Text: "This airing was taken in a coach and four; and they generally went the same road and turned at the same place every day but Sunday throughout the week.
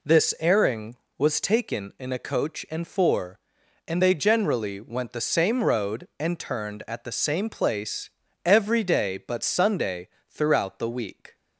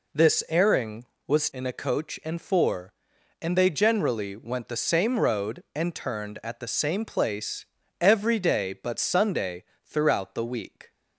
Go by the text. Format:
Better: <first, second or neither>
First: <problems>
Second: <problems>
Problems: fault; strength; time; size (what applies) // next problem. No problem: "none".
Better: first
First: pauses between "place" and "every"; slight; at 8.0 s; 0.36 s long // pauses between "Sunday" and "throughout"; slight; at 10.0 s; 0.22 s long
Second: skips "taken"; at 1.5 s // pauses between "place" and "every"; slight; at 7.6 s; 0.36 s long // pauses between "Sunday" and "throughout"; slight; at 9.6 s; 0.22 s long